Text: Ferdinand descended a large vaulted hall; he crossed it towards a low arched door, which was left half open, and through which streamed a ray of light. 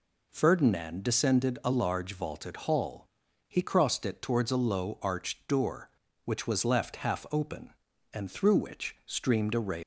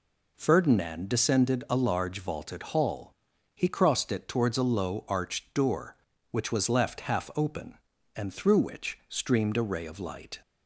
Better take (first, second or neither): second